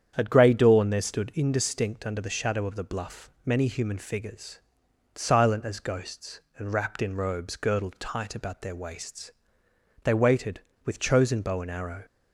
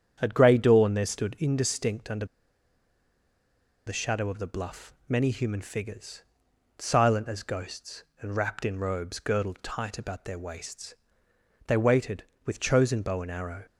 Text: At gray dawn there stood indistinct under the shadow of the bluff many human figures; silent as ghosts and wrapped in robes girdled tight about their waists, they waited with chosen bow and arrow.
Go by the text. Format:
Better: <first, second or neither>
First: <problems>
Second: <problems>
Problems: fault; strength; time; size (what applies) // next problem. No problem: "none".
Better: first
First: starts louder than the rest; strong; until 1.1 s; 8.5 dB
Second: starts louder than the rest; strong; until 1.2 s; 8.5 dB // pauses between "under" and "the"; strong; at 2.2 s; 1.6 s long